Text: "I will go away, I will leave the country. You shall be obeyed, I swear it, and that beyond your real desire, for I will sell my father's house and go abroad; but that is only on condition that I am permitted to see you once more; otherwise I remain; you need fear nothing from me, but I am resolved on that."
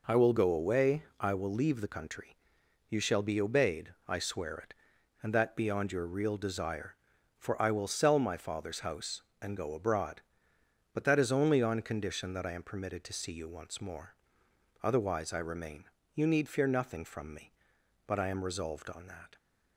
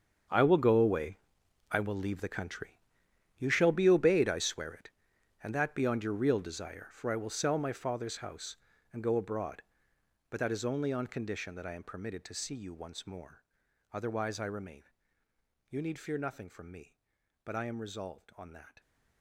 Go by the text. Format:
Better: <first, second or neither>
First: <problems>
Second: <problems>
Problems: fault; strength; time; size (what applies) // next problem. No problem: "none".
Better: first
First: none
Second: gets quieter; strong; throughout; 15 dB